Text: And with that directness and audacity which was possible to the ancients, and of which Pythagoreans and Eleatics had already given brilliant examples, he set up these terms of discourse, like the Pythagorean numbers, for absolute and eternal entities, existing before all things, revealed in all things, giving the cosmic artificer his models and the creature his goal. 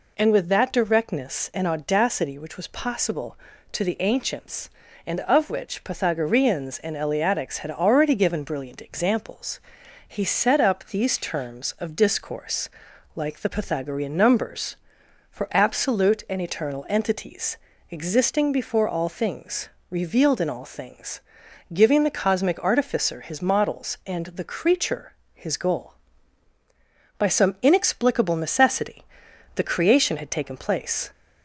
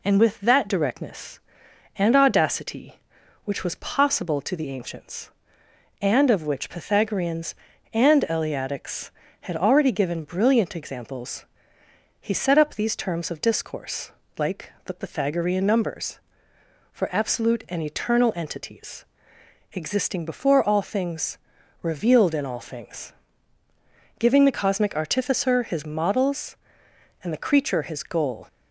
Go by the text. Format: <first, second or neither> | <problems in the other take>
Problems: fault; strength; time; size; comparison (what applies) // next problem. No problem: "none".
second | pauses between "creature" and "his"; slight; at 25.1 s; 0.20 s long // goes on to say "By some inexplicable necessity the creation had taken place"; strong; from 27.1 s on; 3.9 s long